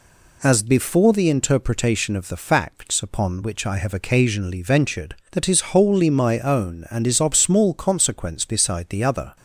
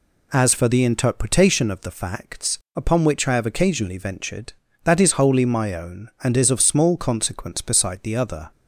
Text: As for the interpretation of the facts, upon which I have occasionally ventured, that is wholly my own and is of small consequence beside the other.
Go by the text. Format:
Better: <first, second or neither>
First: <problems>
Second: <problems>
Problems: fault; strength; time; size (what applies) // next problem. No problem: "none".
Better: second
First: says "before" for "for"; at 0.6 s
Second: none